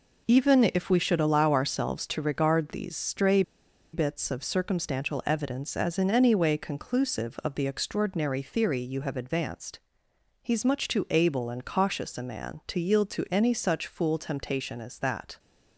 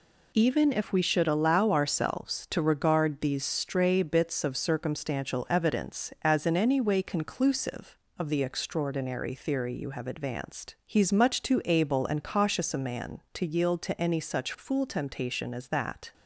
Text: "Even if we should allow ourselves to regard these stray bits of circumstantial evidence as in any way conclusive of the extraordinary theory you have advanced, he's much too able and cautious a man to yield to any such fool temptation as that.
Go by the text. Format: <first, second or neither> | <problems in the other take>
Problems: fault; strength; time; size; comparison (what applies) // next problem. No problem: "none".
second | pauses between "stray" and "bits"; noticeable; at 3.4 s; 0.51 s long